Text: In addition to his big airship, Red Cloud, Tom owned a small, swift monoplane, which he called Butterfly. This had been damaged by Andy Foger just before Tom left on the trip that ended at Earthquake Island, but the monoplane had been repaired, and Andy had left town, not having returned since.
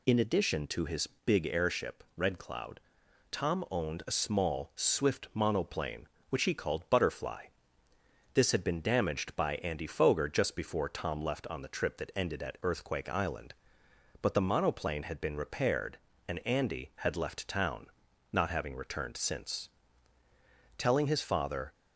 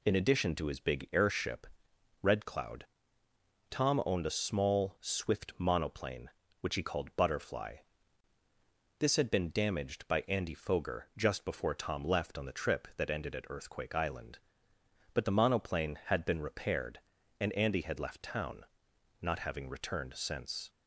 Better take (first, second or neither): second